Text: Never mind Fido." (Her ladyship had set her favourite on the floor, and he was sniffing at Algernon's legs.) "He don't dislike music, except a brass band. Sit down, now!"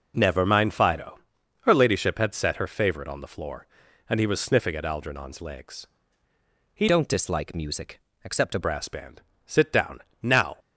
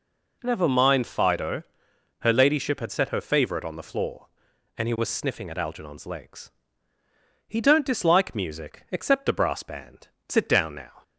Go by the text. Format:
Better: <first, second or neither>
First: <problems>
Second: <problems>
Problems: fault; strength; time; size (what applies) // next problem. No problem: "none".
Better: second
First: changes voice from "don't" to "a"; from 6.8 to 8.5 s; 1.7 s long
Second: none